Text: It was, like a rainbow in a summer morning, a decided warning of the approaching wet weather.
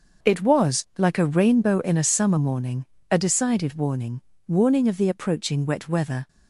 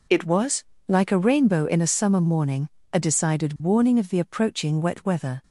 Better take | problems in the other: second | says "warning" twice; at 4.4 s

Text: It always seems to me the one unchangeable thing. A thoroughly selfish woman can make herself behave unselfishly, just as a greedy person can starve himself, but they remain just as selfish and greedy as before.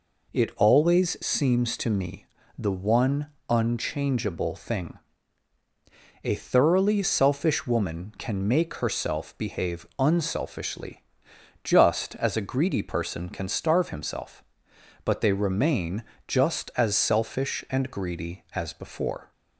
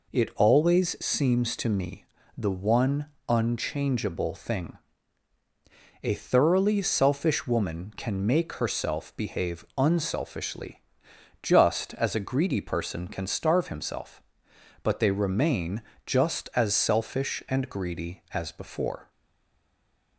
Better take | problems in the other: first | pauses between "me" and "the"; slight; at 2.0 s; 0.32 s long; slight in the first // pauses between "one" and "unchangeable"; slight; at 3.0 s; 0.20 s long; slight in the first // pauses between "remain" and "just"; slight; at 15.8 s; 0.24 s long; slight in the first // stays silent after the last word; from 19.0 s on; 1.1 s long

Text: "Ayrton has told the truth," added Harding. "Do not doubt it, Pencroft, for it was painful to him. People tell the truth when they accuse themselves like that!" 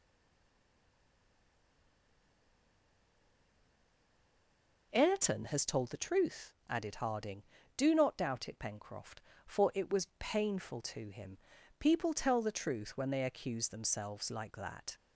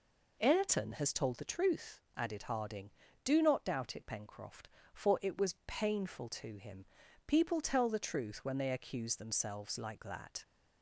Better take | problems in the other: second | stays silent before the first word; strong; until 4.9 s; 4.9 s long

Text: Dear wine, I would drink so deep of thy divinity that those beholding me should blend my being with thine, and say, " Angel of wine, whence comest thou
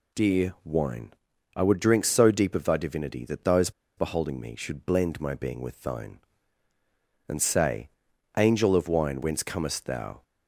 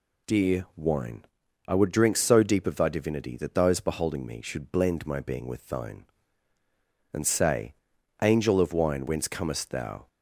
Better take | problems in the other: second | pauses between "those" and "beholding"; slight; at 3.7 s; 0.26 s long

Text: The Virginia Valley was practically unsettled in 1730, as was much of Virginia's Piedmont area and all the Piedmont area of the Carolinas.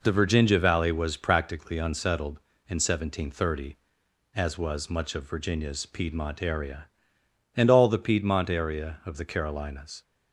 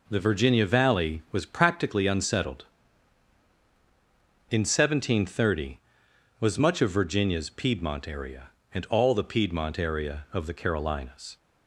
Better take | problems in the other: first | skips "as"; at 6.0 s

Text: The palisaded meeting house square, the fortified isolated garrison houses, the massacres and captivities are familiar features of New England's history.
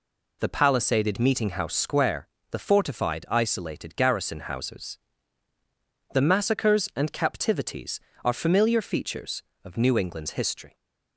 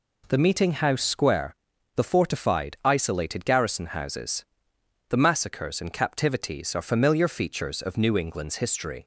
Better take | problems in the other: first | skips "palisaded"; at 0.3 s

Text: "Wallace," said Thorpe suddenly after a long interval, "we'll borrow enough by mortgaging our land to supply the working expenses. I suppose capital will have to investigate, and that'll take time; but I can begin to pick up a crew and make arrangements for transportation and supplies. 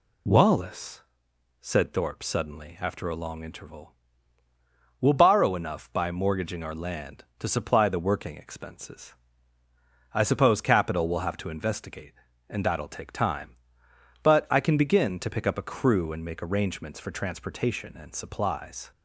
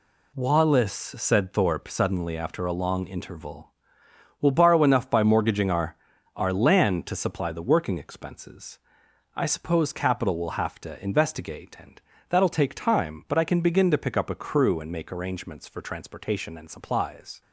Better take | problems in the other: first | says "our" twice; at 6.3 s // pauses between "and" and "that'll"; slight; at 12.0 s; 0.28 s long

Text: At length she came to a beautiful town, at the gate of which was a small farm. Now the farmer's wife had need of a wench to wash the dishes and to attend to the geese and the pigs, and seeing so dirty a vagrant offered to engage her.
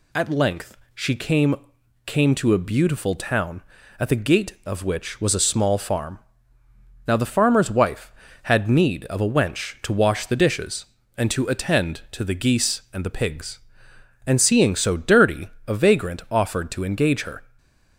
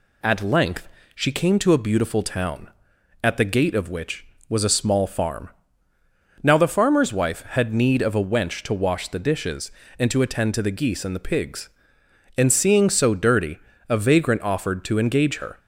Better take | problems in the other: second | pauses between "length" and "she"; slight; at 0.7 s; 0.18 s long; slight in the second // says "came" twice; at 2.0 s // pauses between "dirty" and "a"; slight; at 15.4 s; 0.20 s long; slight in the second

